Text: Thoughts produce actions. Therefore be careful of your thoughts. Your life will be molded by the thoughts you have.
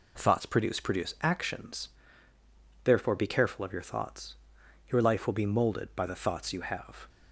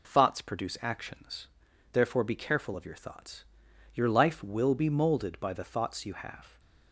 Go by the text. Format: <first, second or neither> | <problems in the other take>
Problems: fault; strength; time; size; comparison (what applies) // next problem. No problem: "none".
second | says "produce" twice; at 0.8 s